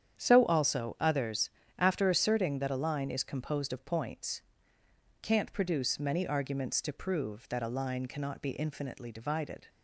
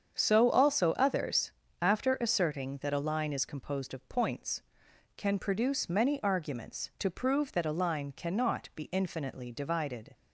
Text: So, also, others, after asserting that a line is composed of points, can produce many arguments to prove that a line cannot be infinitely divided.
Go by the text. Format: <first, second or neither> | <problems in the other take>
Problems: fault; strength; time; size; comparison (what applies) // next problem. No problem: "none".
second | starts louder than the rest; strong; until 1.2 s; 8.5 dB; strong in the second // says "can't" for "can"; at 5.1 s